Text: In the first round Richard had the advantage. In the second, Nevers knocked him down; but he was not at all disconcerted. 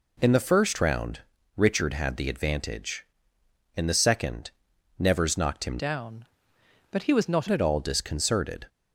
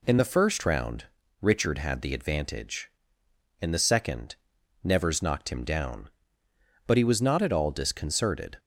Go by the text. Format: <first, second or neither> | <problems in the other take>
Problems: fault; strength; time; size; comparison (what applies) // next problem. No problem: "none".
second | pauses between "round" and "Richard"; slight; at 1.2 s; 0.36 s long; slight in the second // changes voice from "down" to "not"; from 5.7 to 7.4 s; 1.7 s long